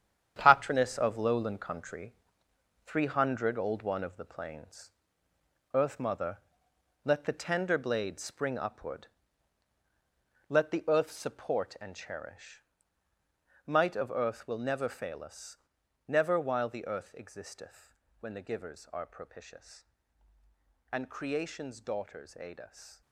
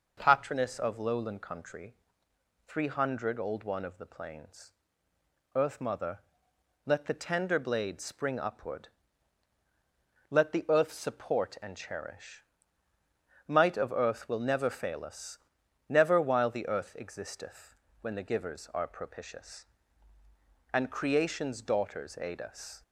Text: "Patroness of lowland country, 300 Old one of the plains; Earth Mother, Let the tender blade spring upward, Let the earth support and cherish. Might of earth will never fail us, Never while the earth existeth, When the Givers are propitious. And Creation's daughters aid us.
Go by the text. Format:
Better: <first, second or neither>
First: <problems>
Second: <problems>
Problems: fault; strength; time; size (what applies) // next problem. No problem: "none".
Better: second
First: gets quieter; strong; throughout; 10 dB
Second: none